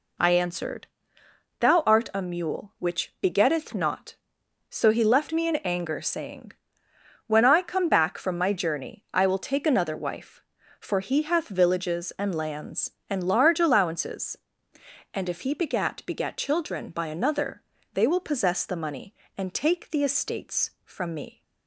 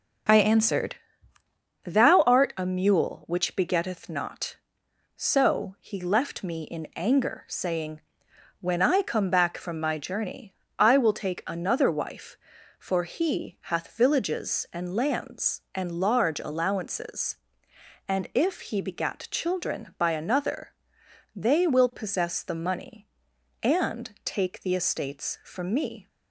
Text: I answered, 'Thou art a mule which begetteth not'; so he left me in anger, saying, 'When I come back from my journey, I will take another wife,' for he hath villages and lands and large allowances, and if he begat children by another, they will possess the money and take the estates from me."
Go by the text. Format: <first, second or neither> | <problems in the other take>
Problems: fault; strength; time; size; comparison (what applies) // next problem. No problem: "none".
second | says "begat" twice; at 16.0 s